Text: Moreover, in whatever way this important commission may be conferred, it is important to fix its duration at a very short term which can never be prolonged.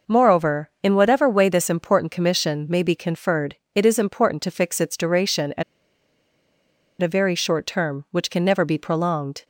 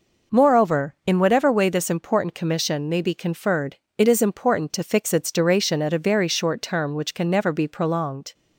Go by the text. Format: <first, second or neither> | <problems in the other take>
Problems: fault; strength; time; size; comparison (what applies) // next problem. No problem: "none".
second | pauses between "at" and "a"; strong; at 5.6 s; 1.3 s long